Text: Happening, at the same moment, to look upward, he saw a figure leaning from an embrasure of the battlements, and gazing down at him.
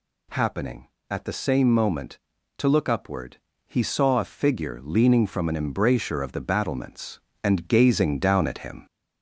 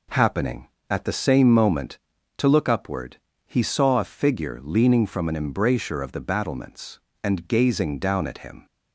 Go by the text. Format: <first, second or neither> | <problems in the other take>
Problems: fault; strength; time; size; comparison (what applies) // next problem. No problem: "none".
second | gets louder; throughout; 3.5 dB